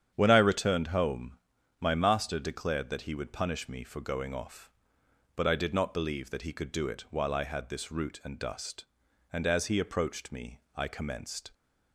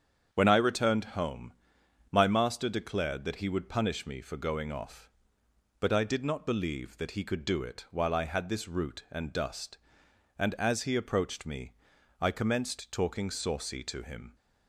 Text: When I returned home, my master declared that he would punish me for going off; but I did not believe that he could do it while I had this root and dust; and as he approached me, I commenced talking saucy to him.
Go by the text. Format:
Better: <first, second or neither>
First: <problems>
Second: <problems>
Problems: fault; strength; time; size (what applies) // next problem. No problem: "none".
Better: second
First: starts louder than the rest; strong; until 1.1 s; 9 dB // stops before "talking saucy to him"; at 11.5 s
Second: starts louder than the rest; strong; until 1.3 s; 7.5 dB